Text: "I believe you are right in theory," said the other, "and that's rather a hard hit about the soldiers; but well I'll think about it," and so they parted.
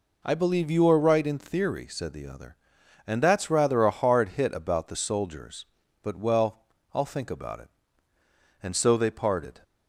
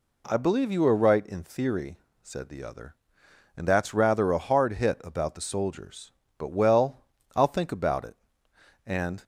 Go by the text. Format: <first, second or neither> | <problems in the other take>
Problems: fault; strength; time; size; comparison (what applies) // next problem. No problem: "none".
first | pauses between "well" and "I'll"; slight; at 7.0 s; 0.34 s long; slight in the first // stops before "so they parted"; at 9.2 s